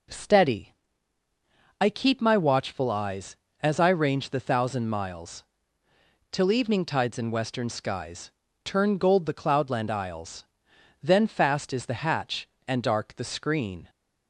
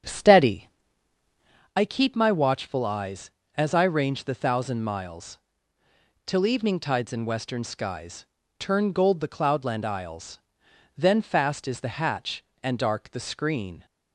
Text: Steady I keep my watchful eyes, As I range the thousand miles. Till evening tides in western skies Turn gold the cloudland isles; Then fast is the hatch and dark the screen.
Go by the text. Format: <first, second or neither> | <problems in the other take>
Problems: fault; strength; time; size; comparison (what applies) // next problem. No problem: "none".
first | starts louder than the rest; strong; until 1.7 s; 8 dB // pauses between "Steady" and "I"; at 0.6 s; 1.0 s long; also in the first // pauses between "skies" and "Turn"; slight; at 8.2 s; 0.32 s long; slight in the first